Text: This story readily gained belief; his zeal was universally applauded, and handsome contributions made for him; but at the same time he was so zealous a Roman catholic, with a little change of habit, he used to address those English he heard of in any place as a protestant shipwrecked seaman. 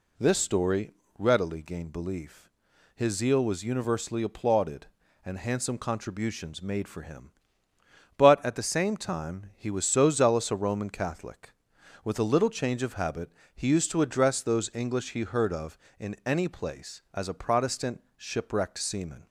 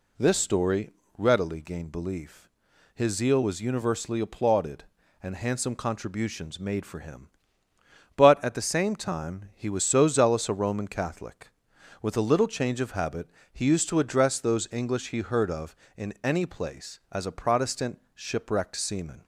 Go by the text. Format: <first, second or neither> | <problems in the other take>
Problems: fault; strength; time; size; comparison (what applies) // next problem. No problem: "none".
neither | pauses between "story" and "readily"; slight; the same in both // pauses between "protestant" and "shipwrecked"; slight; the same in both